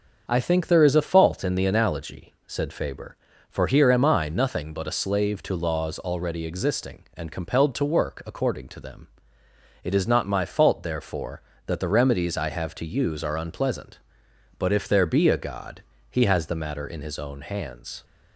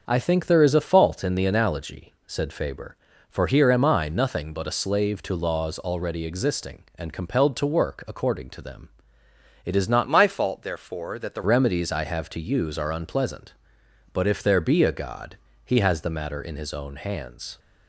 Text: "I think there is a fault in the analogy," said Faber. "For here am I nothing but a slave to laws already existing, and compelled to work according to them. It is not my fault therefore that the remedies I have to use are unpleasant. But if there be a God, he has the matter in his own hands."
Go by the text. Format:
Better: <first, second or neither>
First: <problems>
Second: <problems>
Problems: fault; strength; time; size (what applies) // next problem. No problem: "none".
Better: first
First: starts louder than the rest; until 1.2 s; 6.5 dB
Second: starts louder than the rest; until 1.0 s; 6.5 dB // changes voice from "my" to "the"; from 10.0 to 11.4 s; 1.4 s long